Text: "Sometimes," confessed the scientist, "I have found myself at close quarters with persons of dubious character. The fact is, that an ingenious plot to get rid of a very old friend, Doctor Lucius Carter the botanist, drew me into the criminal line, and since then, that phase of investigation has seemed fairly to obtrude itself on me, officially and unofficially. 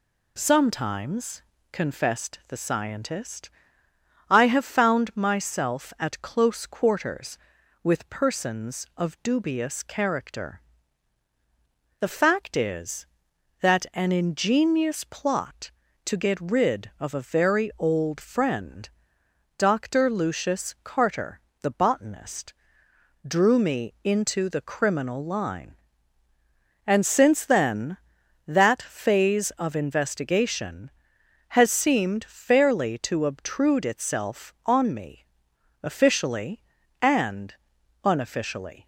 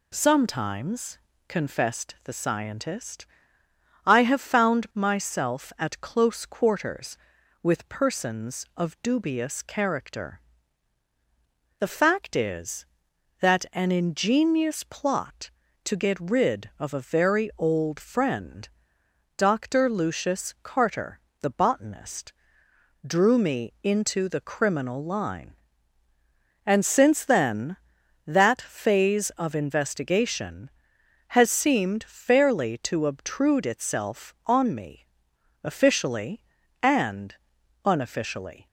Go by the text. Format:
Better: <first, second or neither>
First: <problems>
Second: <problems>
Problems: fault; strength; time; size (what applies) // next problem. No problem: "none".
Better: neither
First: pauses between "Carter" and "the"; slight; at 21.4 s; 0.22 s long // pauses between "and" and "unofficially"; noticeable; at 37.5 s; 0.48 s long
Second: pauses between "Carter" and "the"; slight; at 21.2 s; 0.22 s long // pauses between "and" and "unofficially"; noticeable; at 37.3 s; 0.48 s long